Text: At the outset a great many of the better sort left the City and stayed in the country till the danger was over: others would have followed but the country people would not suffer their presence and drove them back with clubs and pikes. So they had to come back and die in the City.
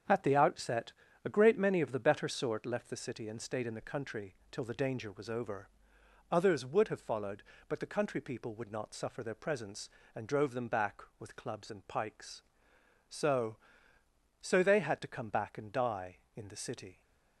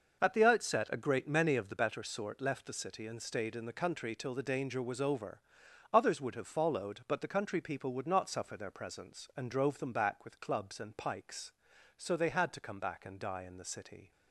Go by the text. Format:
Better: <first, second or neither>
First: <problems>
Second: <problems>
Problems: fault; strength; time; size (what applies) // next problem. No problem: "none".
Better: second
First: starts louder than the rest; strong; until 1.4 s; 7.5 dB // pauses between "outset" and "a"; slight; at 0.9 s; 0.32 s long // pauses between "country" and "till"; slight; at 4.3 s; 0.16 s long // says "So" twice; at 14.4 s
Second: none